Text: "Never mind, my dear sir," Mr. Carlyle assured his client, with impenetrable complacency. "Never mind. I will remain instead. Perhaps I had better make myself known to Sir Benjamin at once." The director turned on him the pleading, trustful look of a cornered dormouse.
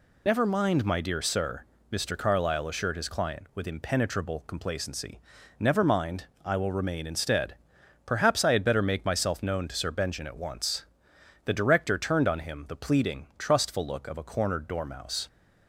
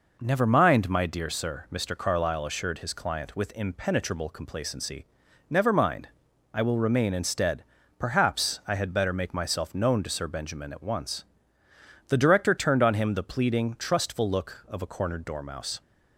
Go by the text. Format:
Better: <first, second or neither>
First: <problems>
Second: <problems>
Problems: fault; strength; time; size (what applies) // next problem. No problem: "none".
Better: second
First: loses the start of "Never"; at 0.2 s; 40 ms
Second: none